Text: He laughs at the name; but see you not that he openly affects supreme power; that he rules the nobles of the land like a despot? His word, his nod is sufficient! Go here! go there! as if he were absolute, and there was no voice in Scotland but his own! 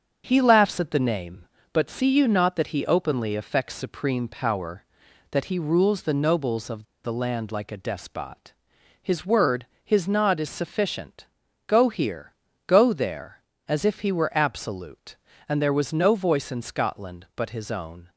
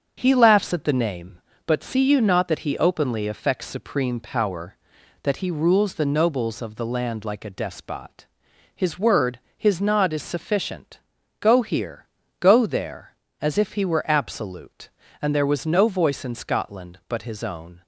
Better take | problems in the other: second | starts louder than the rest; until 1.2 s; 7 dB; strong in the second // pauses between "of" and "the"; slight; at 6.8 s; 0.20 s long

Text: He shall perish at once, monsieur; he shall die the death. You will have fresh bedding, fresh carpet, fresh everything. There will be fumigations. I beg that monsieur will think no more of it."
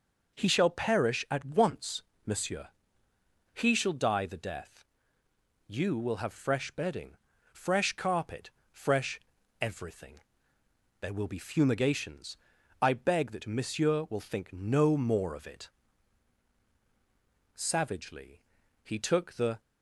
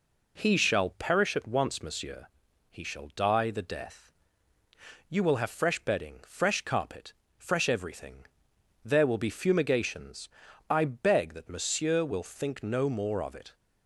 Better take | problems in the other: second | pauses between "fresh" and "everything"; at 9.2 s; 0.40 s long // goes on to say "Savagely he took the"; strong; from 17.5 s on; 2.0 s long

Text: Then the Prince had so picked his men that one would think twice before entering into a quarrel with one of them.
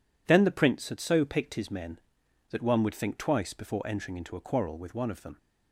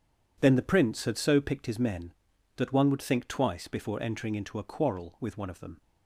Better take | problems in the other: neither | none

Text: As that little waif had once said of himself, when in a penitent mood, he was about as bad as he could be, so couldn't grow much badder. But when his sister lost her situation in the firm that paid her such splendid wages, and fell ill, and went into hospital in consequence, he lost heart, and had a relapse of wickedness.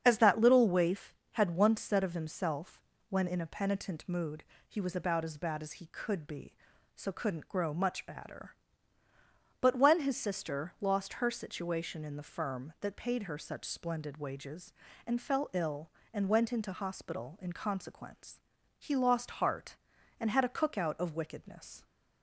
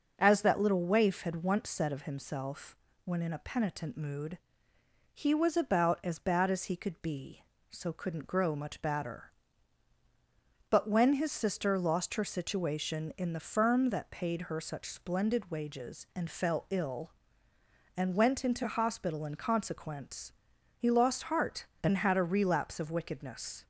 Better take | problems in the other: second | starts louder than the rest; strong; until 1.0 s; 7.5 dB; also in the second // says "cookout" for "relapse"; at 20.5 s

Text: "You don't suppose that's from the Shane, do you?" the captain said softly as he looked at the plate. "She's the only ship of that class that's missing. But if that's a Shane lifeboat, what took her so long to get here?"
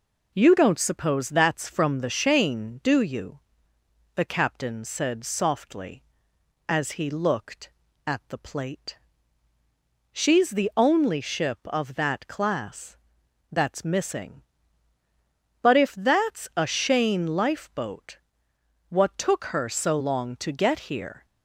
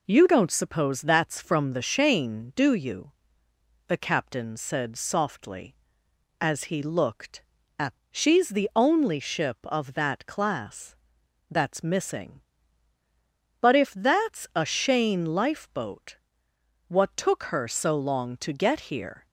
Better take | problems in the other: first | skips "the plate"; at 8.0 s // pauses between "class" and "that's"; noticeable; at 10.9 s; 0.54 s long; noticeable in the first

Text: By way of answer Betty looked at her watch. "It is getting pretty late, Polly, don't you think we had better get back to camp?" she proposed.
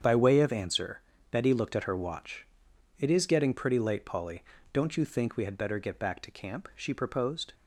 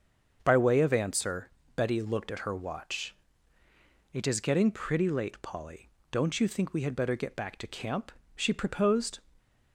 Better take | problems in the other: neither | starts louder than the rest; the same in both // pauses between "answer" and "Betty"; slight; the same in both

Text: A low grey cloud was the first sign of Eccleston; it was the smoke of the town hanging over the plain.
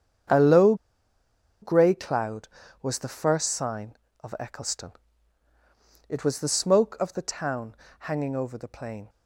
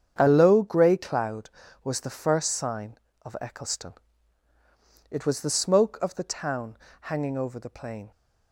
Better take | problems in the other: second | starts louder than the rest; strong; until 2.1 s; 8 dB; strong in the second // pauses between "low" and "grey"; noticeable; at 0.7 s; 0.87 s long // pauses between "town" and "hanging"; slight; at 7.7 s; 0.24 s long; slight in the second

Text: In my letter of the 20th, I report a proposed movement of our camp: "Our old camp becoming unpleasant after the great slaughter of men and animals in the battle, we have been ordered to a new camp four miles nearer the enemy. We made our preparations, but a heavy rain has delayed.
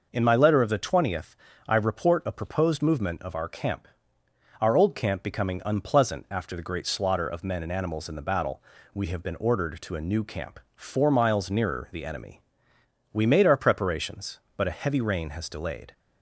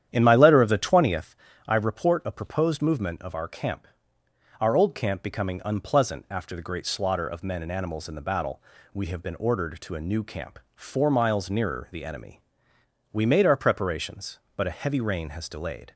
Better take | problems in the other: first | starts louder than the rest; strong; until 1.4 s; 10 dB

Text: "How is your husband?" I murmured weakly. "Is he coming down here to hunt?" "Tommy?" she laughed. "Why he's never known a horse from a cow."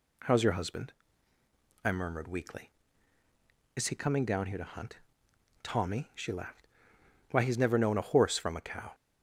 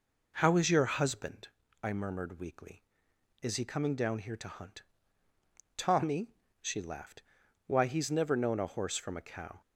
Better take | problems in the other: first | starts louder than the rest; noticeable; until 1.5 s; 4.5 dB

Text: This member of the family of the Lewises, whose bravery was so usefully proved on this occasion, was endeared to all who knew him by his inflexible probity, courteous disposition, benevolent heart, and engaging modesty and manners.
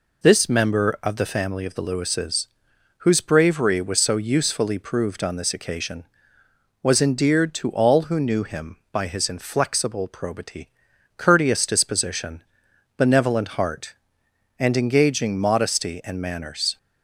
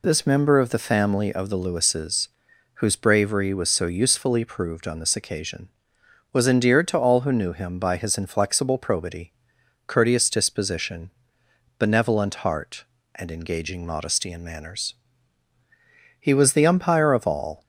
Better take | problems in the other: first | goes on to say "He was the umpire of all"; from 16.2 s on; 1.4 s long

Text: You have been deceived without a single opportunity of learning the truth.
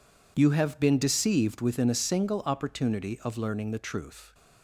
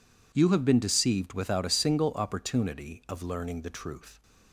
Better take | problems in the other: second | says "within" for "without"; at 1.6 s

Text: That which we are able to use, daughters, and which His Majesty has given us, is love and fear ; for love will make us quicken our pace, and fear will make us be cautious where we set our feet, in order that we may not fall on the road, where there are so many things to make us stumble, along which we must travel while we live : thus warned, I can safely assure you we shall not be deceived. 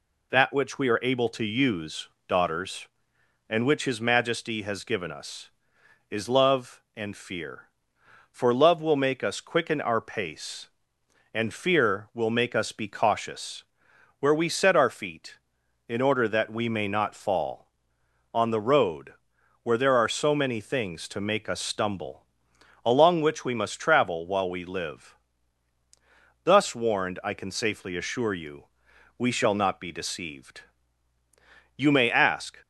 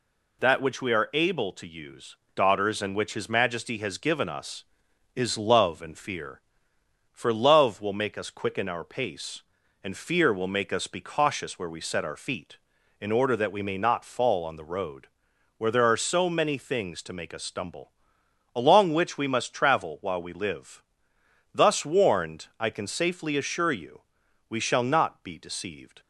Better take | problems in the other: second | pauses between "cautious" and "where"; noticeable; at 13.6 s; 0.58 s long // pauses between "you" and "we"; noticeable; at 28.6 s; 0.52 s long; noticeable in the second // goes on to say "You may ask"; noticeable; from 31.7 s on; 0.84 s long

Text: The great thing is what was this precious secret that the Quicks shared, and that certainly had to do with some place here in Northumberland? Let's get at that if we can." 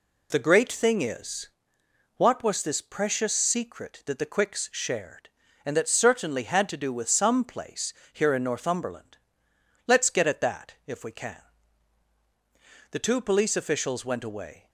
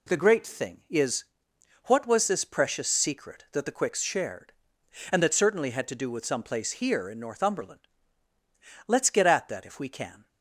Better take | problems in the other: second | pauses between "is" and "what"; noticeable; at 1.4 s; 0.66 s long; noticeable in the second // pauses between "place" and "here"; slight; at 7.9 s; 0.22 s long // goes on to say "The two police officials went away"; strong; from 12.9 s on; 1.7 s long

